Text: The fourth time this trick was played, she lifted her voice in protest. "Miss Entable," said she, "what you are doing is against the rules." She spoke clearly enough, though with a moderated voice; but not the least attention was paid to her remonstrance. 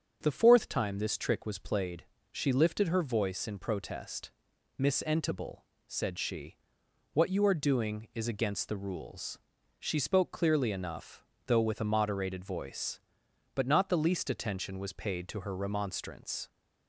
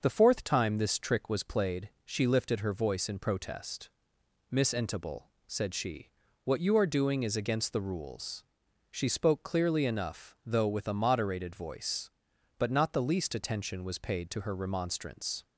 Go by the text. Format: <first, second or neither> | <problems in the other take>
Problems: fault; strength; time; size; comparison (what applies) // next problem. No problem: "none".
neither | starts louder than the rest; the same in both